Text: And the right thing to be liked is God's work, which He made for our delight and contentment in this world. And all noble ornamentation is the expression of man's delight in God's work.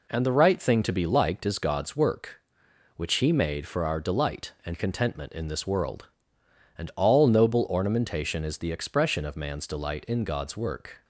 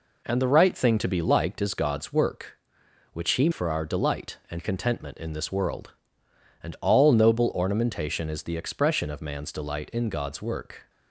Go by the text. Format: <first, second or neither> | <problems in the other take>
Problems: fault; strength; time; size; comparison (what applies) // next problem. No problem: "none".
first | skips "made"; at 3.5 s